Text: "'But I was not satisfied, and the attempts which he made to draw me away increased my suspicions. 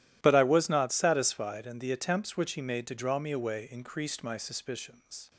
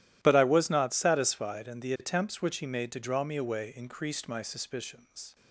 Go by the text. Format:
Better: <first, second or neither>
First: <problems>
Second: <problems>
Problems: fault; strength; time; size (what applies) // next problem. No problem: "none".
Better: neither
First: starts louder than the rest; strong; until 1.2 s; 13.5 dB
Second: starts louder than the rest; strong; until 1.2 s; 13.5 dB